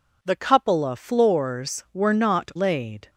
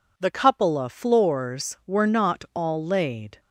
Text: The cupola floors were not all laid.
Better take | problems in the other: second | skips "all"; at 2.5 s

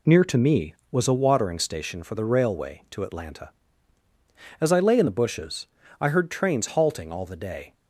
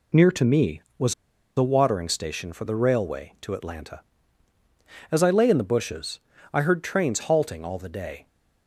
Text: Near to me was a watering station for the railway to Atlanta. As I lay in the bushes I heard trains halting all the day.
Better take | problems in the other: first | pauses between "was" and "a"; at 1.1 s; 0.43 s long // pauses between "bushes" and "I"; slight; at 6.1 s; 0.36 s long; slight in the first

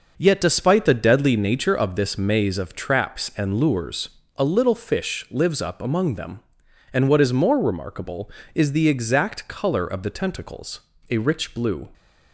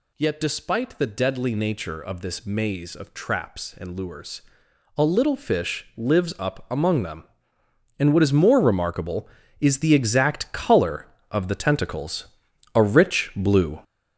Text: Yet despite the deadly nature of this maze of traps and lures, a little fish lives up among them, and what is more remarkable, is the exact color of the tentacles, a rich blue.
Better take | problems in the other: first | gets louder; throughout; 7 dB

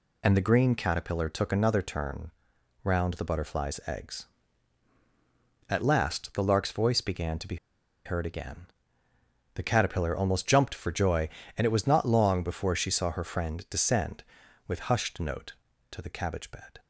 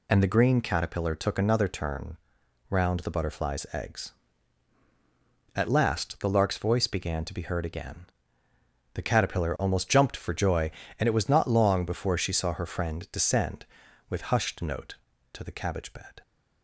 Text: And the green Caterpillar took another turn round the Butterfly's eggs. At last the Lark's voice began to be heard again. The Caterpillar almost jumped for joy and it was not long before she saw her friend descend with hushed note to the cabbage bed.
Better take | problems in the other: second | pauses between "turn" and "round"; noticeable; at 2.3 s; 0.52 s long; noticeable in the second // pauses between "be" and "heard"; noticeable; at 7.5 s; 0.49 s long

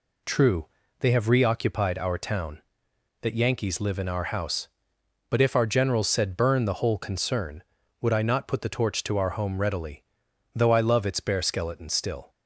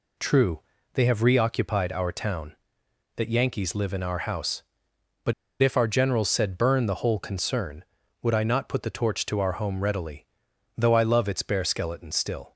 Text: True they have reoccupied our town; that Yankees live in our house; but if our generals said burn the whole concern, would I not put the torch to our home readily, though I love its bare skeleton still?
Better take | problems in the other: first | pauses between "True" and "they"; slight; at 0.6 s; 0.34 s long; slight in the first // pauses between "but" and "if"; slight; at 5.3 s; 0.29 s long

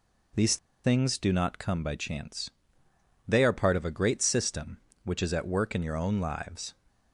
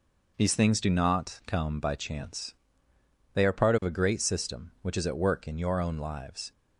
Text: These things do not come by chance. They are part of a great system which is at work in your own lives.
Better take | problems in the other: second | pauses between "These" and "things"; slight; at 0.5 s; 0.27 s long

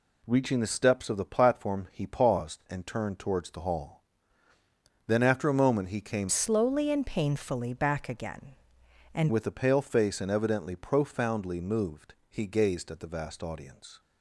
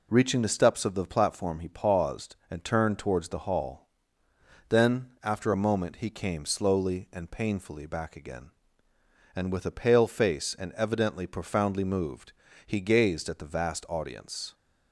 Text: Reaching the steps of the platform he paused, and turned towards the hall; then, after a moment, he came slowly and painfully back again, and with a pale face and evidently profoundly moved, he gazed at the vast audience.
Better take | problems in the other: second | changes voice from "slowly" to "and"; from 6.2 to 9.3 s; 3.1 s long

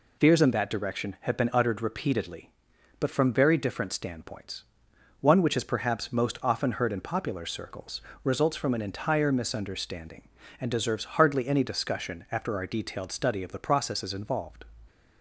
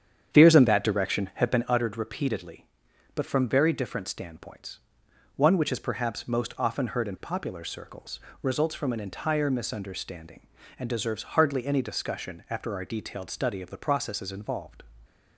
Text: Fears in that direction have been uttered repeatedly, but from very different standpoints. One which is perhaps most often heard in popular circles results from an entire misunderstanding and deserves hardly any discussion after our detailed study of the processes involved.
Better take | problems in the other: first | starts louder than the rest; strong; until 1.7 s; 8.5 dB // pauses between "circles" and "results"; slight; at 8.1 s; 0.22 s long; slight in the first

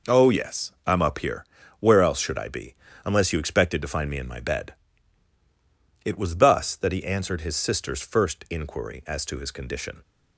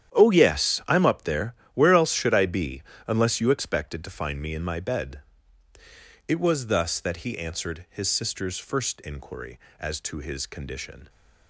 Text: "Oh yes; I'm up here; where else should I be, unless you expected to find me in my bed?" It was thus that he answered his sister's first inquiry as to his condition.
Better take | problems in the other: first | starts louder than the rest; strong; until 1.1 s; 10 dB // says "there" for "here"; at 1.2 s

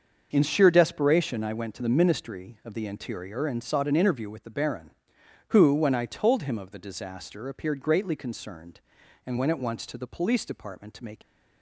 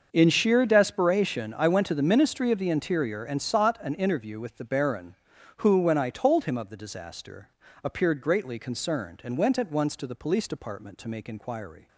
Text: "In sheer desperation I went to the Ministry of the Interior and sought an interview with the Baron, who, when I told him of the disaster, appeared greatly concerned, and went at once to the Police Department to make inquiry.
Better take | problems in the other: second | starts louder than the rest; until 1.3 s; 6.5 dB; also in the second // stops before "inquiry"; at 11.2 s

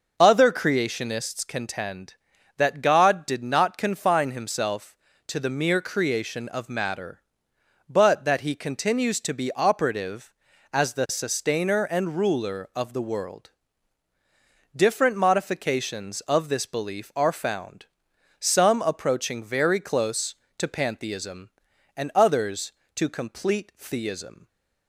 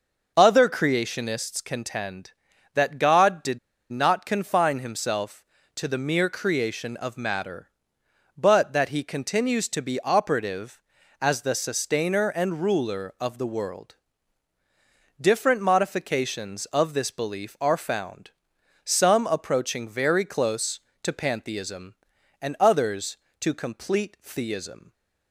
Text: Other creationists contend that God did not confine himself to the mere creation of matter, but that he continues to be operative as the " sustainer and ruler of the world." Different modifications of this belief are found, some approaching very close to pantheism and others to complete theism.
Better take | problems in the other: first | starts louder than the rest; until 1.3 s; 6 dB; noticeable in the first // pauses between "did" and "not"; slight; at 3.5 s; 0.31 s long

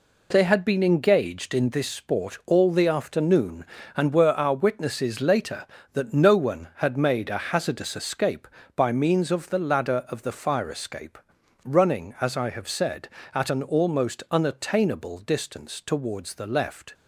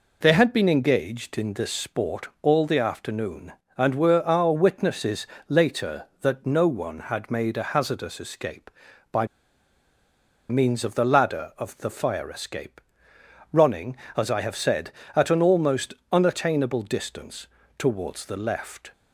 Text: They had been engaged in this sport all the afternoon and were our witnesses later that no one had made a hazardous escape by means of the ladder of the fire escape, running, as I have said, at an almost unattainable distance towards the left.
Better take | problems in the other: first | pauses between "witnesses" and "later"; slight; at 5.2 s; 0.22 s long // pauses between "by" and "means"; at 9.2 s; 1.2 s long // pauses between "almost" and "unattainable"; slight; at 15.9 s; 0.22 s long // pauses between "distance" and "towards"; slight; at 17.4 s; 0.32 s long

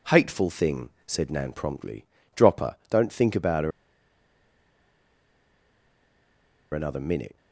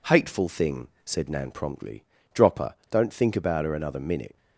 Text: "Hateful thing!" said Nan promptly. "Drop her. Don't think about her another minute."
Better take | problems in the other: second | pauses between "her" and "another"; strong; at 3.7 s; 3.0 s long

